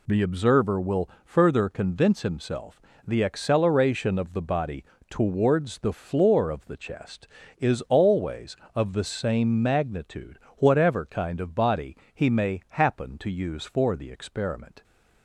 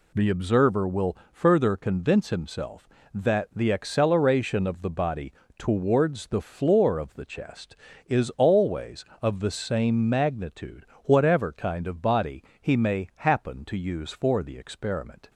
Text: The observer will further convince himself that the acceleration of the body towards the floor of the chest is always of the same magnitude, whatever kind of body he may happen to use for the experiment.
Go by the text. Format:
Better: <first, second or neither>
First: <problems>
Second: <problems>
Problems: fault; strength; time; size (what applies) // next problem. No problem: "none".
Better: second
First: pauses between "will" and "further"; slight; at 1.0 s; 0.16 s long // skips "that"; at 2.9 s // pauses between "body" and "towards"; slight; at 4.8 s; 0.26 s long // pauses between "body" and "he"; slight; at 11.9 s; 0.18 s long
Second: pauses between "will" and "further"; slight; at 1.1 s; 0.16 s long // pauses between "body" and "towards"; slight; at 5.3 s; 0.26 s long // pauses between "body" and "he"; slight; at 12.4 s; 0.18 s long